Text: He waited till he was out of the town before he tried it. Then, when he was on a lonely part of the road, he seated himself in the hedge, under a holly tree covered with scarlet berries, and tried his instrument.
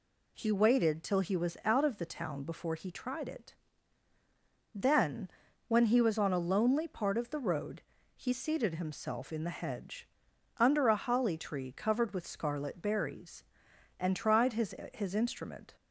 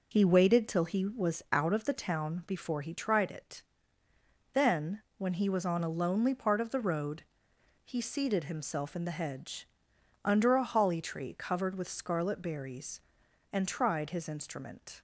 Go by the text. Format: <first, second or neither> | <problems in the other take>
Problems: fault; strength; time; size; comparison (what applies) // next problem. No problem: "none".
second | says "his" twice; at 14.9 s